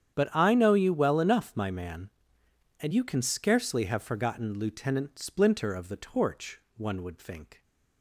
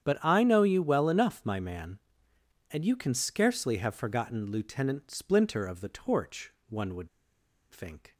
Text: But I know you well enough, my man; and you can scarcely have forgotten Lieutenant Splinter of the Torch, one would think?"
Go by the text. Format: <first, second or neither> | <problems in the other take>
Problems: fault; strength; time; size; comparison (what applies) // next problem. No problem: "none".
first | starts louder than the rest; strong; until 1.0 s; 9 dB; strong in the first // pauses between "would" and "think"; noticeable; at 7.0 s; 0.63 s long